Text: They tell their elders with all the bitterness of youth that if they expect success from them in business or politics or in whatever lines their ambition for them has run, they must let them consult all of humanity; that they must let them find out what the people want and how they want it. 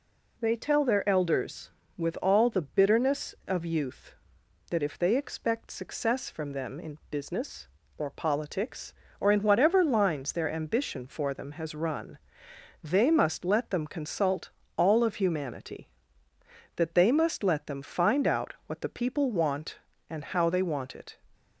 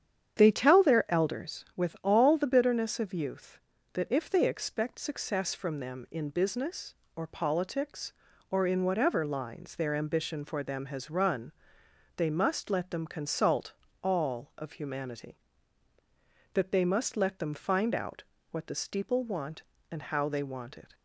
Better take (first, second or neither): first